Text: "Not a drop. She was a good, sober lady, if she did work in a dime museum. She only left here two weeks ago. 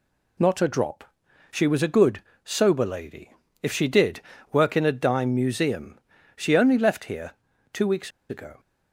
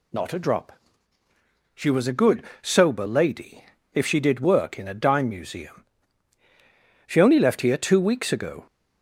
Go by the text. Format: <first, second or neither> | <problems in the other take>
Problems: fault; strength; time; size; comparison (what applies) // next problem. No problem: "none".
second | pauses between "did" and "work"; slight; at 4.2 s; 0.30 s long // pauses between "here" and "two"; at 7.3 s; 0.42 s long // pauses between "weeks" and "ago"; slight; at 8.1 s; 0.19 s long